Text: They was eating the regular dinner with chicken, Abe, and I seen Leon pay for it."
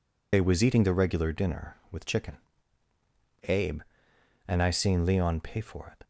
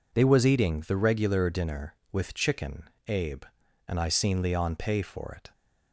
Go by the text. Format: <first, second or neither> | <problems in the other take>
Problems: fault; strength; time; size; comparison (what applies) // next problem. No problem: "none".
second | loses the start of "They"; at 0.3 s; 55 ms